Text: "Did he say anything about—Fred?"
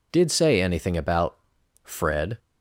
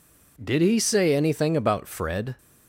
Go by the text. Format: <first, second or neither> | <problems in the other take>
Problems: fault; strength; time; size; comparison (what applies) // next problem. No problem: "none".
second | skips "he"; at 0.3 s